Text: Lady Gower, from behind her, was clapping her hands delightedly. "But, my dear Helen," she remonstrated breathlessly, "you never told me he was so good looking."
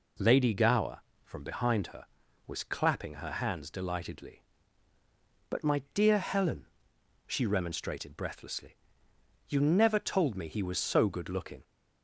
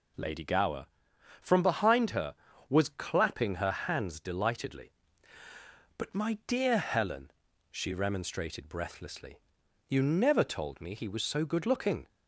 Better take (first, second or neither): neither